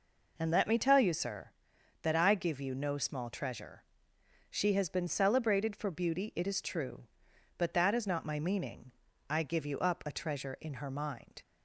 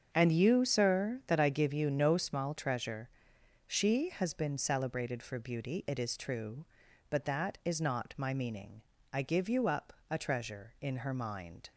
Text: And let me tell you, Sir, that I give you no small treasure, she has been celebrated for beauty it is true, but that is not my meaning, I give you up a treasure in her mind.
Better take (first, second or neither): first